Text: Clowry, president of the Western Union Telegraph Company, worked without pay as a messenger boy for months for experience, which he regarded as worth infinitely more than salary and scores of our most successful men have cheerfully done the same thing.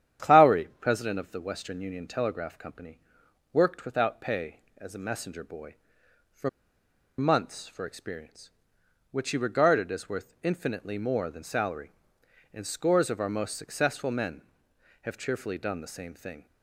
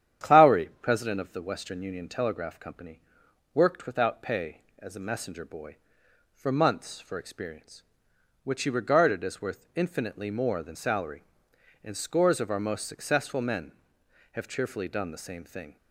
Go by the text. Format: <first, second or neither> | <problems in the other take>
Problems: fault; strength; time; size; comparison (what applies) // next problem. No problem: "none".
second | starts louder than the rest; strong; until 1.3 s; 9.5 dB; strong in the second // pauses between "for" and "months"; noticeable; at 6.4 s; 0.69 s long